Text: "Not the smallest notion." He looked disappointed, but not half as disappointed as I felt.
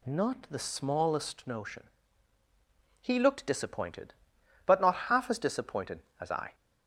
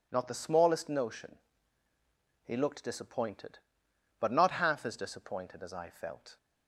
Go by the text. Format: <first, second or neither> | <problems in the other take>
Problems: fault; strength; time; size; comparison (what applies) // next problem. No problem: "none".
second | stops before "felt"; at 6.5 s